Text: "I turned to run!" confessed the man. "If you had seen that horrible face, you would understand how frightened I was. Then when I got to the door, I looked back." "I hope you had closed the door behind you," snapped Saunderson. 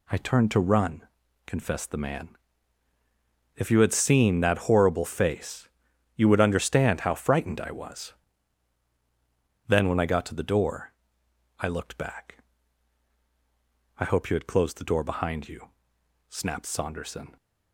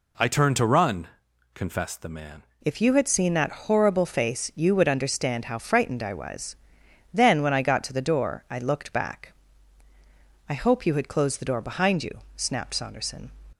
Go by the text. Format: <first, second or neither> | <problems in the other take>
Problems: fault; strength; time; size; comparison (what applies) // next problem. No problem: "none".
first | changes voice at "If"; from 2.6 s on; 10.7 s long